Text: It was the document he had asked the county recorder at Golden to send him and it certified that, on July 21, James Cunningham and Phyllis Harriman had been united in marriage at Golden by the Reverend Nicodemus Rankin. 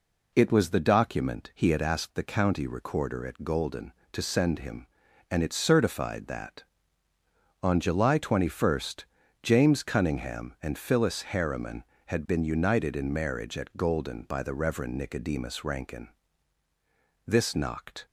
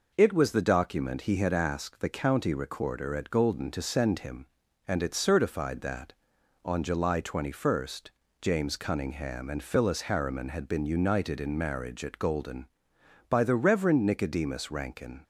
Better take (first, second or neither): second